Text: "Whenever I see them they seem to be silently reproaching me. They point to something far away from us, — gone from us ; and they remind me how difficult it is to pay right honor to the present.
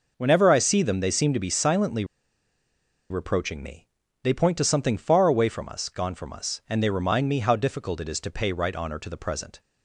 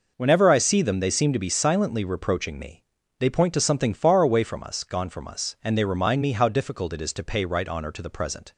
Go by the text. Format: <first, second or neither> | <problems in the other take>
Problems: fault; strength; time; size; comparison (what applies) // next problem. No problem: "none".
second | pauses between "silently" and "reproaching"; at 2.0 s; 1.0 s long